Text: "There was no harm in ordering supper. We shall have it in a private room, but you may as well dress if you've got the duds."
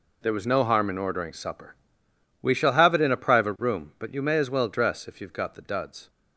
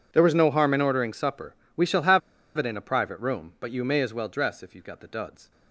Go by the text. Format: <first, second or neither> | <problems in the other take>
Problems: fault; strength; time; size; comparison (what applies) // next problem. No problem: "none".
first | pauses between "have" and "it"; at 2.2 s; 0.38 s long